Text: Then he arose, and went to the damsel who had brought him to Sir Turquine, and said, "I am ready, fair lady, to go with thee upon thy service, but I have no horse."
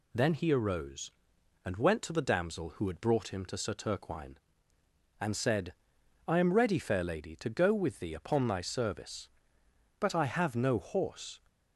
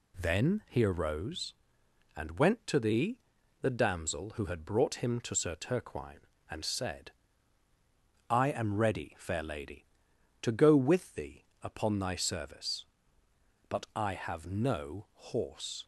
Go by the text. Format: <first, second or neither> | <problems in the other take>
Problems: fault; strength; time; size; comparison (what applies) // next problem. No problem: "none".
first | says "the" twice; at 3.6 s // pauses between "thee" and "upon"; slight; at 11.4 s; 0.18 s long